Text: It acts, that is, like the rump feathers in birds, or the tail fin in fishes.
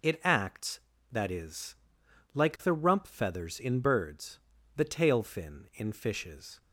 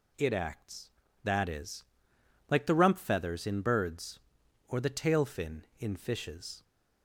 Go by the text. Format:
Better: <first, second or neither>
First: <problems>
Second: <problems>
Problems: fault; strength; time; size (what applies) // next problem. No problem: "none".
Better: second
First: skips "or"; at 4.5 s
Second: none